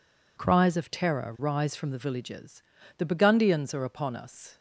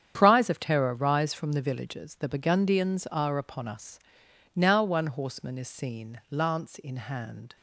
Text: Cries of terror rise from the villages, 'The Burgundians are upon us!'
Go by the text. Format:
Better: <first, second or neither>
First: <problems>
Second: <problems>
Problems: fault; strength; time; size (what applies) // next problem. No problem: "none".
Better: first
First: none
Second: starts louder than the rest; strong; until 1.1 s; 8.5 dB // goes on to say "Now one horseman is seen lance in hand"; strong; from 4.5 s on; 3.0 s long